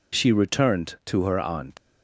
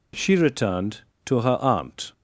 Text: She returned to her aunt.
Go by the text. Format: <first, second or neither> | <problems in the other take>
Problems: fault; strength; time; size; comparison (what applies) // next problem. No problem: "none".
second | leaves "aunt" unfinished; at 1.7 s; 110 ms